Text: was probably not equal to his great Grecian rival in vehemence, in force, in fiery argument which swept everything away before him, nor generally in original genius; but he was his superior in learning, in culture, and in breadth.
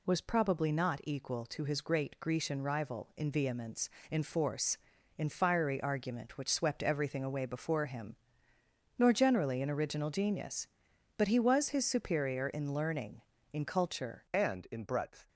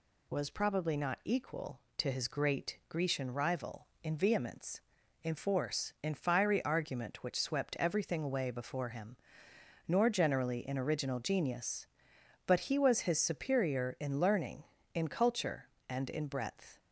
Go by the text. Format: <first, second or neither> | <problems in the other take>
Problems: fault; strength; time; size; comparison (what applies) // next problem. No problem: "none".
second | changes voice at "and"; from 14.3 s on; 0.9 s long